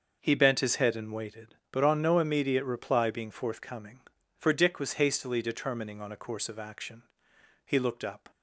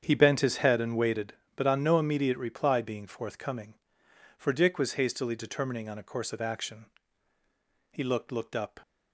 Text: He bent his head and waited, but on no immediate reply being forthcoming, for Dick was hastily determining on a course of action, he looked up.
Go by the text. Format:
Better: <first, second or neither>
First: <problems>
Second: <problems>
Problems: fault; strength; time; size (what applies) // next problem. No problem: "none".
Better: first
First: starts louder than the rest; noticeable; until 1.2 s; 6 dB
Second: starts louder than the rest; strong; until 1.0 s; 8 dB // says "looked" twice; at 8.2 s